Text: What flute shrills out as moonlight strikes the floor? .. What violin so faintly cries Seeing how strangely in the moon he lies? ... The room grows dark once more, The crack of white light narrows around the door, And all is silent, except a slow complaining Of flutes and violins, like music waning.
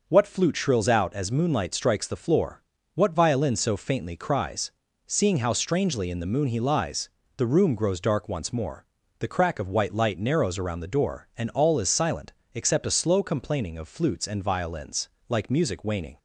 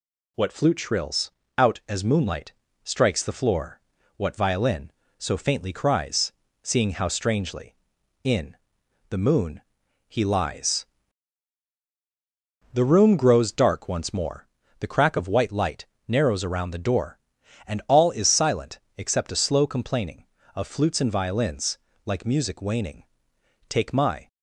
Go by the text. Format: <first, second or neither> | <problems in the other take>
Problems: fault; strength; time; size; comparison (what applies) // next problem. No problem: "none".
first | pauses between "shrills" and "out"; slight; at 1.3 s; 0.26 s long // pauses between "moonlight" and "strikes"; slight; at 2.5 s; 0.32 s long // pauses between "cries" and "Seeing"; slight; at 6.3 s; 0.28 s long; also in the first // pauses between "in" and "the"; noticeable; at 8.5 s; 0.52 s long // pauses between "moon" and "he"; noticeable; at 9.6 s; 0.48 s long // pauses between "light" and "narrows"; slight; at 15.8 s; 0.20 s long // goes on to say "Take my"; from 23.6 s on; 0.58 s long